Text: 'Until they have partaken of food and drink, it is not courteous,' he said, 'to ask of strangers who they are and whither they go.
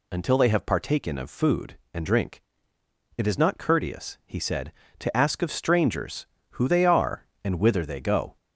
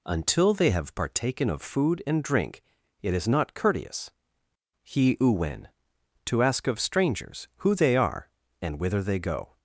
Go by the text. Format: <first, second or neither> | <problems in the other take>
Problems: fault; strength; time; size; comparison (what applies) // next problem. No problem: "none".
first | says "uwen" for "said"; at 5.1 s